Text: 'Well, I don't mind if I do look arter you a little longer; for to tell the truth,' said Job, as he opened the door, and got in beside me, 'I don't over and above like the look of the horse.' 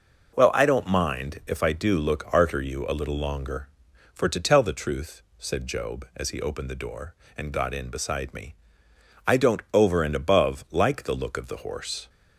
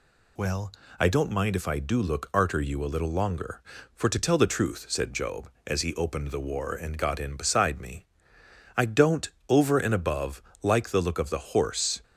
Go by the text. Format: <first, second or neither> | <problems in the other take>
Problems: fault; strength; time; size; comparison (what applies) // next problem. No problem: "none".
first | says "war" for "door"; at 6.3 s // pauses between "don't" and "over"; slight; at 9.2 s; 0.20 s long // pauses between "above" and "like"; slight; at 10.4 s; 0.20 s long